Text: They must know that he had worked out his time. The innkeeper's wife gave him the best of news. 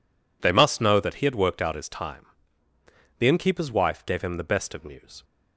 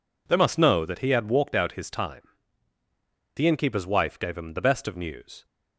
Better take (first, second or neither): first